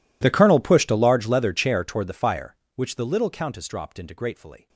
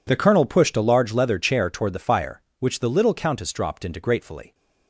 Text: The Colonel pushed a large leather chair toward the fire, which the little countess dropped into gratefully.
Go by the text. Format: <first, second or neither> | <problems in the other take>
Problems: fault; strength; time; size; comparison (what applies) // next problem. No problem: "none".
second | gets quieter; strong; throughout; 26.5 dB